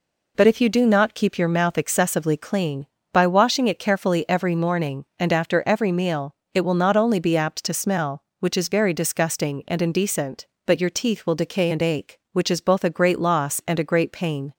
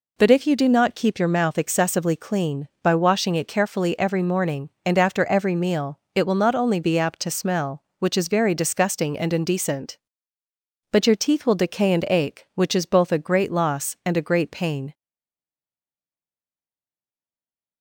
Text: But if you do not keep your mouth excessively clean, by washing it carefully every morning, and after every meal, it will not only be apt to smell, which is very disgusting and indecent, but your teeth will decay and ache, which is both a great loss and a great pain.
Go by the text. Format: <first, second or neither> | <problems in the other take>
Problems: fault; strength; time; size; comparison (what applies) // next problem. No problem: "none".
first | stays silent after the last word; strong; from 14.9 s on; 2.9 s long